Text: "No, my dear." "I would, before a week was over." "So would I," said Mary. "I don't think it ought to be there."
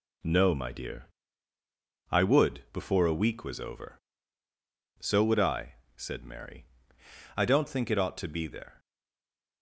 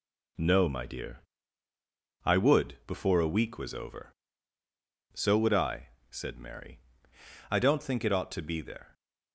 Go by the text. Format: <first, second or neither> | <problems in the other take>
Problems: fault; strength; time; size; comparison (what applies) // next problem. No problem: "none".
second | stays silent after the last word; slight; from 8.7 s on; 0.9 s long